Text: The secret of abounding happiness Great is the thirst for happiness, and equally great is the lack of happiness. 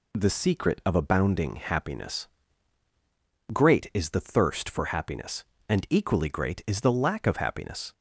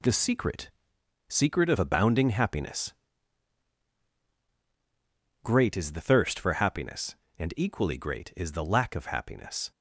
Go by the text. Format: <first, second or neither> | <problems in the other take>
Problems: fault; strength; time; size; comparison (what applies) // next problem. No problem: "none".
first | says "secret" twice; at 1.2 s // pauses between "happiness" and "Great"; strong; at 2.9 s; 2.5 s long; strong in the first